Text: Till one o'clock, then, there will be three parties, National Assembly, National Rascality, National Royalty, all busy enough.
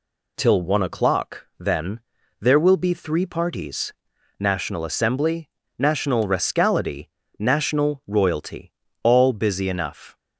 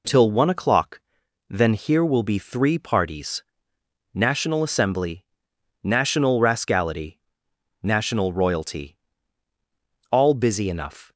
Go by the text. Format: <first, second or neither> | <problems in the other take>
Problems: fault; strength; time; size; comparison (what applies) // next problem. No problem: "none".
first | says "here" for "there"; at 1.7 s